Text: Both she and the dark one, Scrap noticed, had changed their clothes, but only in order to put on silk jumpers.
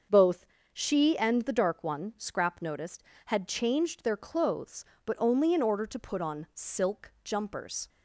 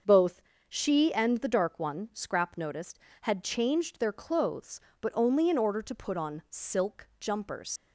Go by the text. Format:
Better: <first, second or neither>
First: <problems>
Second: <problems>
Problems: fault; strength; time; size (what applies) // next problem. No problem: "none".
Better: first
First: starts louder than the rest; until 1.3 s; 6.5 dB // pauses between "Both" and "she"; slight; at 0.4 s; 0.28 s long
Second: starts louder than the rest; until 1.3 s; 6.5 dB // pauses between "Both" and "she"; slight; at 0.4 s; 0.28 s long // leaves "jumpers" unfinished; at 7.7 s; 80 ms